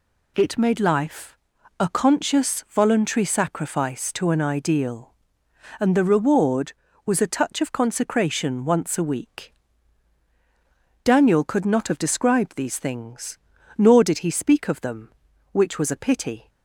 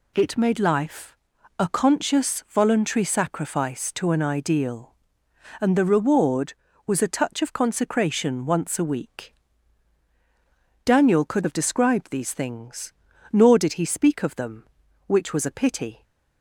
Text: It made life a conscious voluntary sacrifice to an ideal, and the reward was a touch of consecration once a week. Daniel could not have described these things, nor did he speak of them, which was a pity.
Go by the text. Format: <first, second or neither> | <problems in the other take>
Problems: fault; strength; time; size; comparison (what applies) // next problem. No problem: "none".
first | pauses between "life" and "a"; at 1.1 s; 0.42 s long; also in the first // skips "not"; at 11.4 s